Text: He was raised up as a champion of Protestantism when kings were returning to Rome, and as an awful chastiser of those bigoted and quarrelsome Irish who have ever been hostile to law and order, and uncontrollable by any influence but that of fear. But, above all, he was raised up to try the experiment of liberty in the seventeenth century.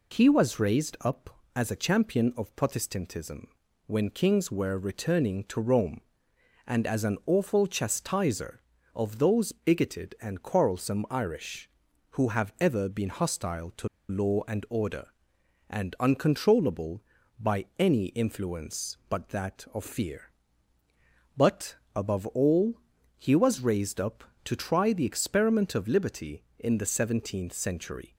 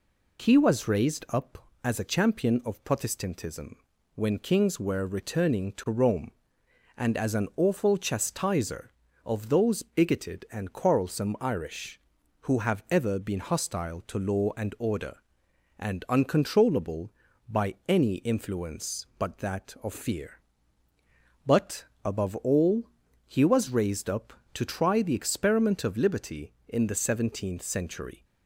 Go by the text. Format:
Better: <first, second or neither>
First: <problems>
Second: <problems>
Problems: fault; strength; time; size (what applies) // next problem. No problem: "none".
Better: second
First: pauses between "Protestantism" and "when"; at 3.4 s; 0.38 s long // pauses between "to" and "law"; slight; at 13.8 s; 0.21 s long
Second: pauses between "Protestantism" and "when"; at 3.7 s; 0.38 s long